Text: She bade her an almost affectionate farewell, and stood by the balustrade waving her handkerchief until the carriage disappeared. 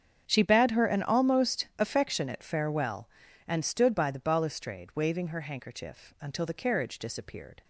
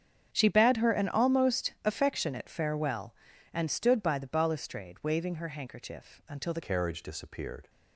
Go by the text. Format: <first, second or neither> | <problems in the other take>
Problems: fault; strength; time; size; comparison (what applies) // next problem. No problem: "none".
first | starts louder than the rest; strong; until 1.3 s; 8 dB; strong in the first // changes voice at "carriage"; from 6.6 s on; 1.0 s long